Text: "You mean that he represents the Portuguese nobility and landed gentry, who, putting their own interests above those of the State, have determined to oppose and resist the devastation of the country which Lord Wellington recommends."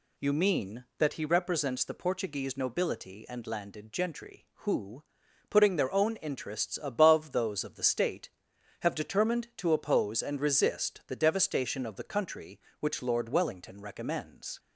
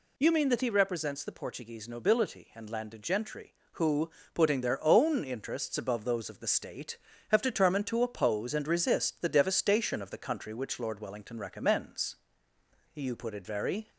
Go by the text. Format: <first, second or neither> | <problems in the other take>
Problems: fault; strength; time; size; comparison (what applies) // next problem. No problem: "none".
first | goes on to say "You put it very"; noticeable; from 12.9 s on; 0.96 s long